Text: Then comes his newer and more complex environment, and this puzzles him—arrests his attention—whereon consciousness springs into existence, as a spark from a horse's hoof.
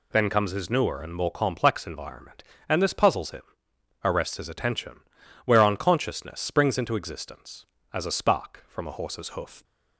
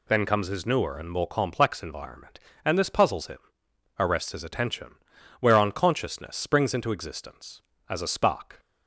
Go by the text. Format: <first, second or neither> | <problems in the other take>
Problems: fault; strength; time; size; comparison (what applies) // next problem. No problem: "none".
first | stops before "from a horse's hoof"; at 8.5 s